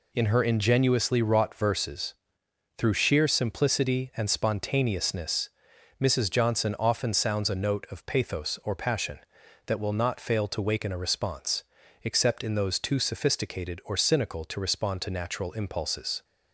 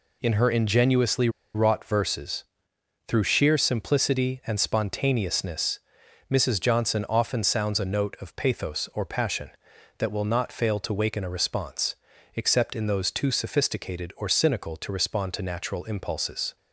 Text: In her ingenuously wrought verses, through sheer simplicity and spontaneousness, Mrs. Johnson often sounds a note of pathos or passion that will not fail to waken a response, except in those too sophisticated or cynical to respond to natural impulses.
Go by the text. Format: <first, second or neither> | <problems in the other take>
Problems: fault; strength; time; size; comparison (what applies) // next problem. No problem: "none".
first | pauses between "ingenuously" and "wrought"; slight; at 1.2 s; 0.25 s long